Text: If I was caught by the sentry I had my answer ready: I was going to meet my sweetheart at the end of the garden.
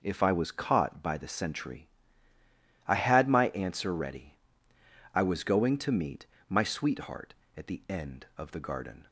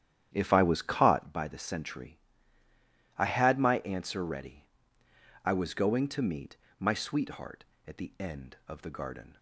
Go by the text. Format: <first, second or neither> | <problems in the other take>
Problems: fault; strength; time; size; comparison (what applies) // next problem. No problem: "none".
first | starts louder than the rest; strong; until 1.3 s; 10.5 dB // pauses between "sentry" and "I"; at 2.1 s; 1.0 s long; also in the first // pauses between "meet" and "my"; slight; at 6.5 s; 0.24 s long; slight in the first